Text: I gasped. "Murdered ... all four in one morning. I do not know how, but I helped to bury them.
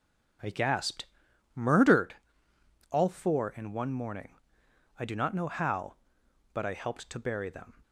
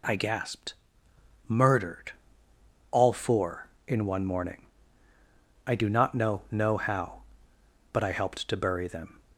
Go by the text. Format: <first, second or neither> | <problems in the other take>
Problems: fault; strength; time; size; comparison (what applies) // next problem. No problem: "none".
first | says "know" twice; at 6.5 s